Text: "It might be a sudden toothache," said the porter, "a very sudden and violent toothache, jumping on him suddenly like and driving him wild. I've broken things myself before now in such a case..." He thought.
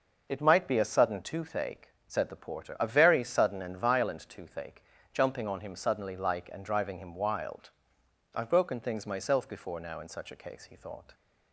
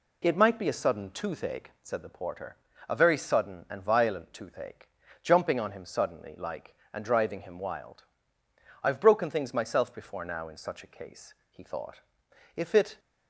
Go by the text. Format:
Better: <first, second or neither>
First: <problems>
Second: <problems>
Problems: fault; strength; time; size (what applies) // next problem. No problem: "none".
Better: first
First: none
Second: goes on to say "If it"; slight; from 12.5 s on; 0.44 s long